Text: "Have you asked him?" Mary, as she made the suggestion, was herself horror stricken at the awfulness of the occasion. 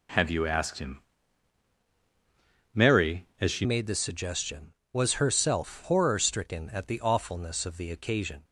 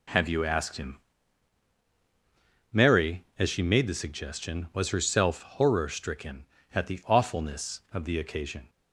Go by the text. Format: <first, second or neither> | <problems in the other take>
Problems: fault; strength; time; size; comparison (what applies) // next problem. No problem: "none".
second | changes voice at "made"; from 3.6 s on; 4.8 s long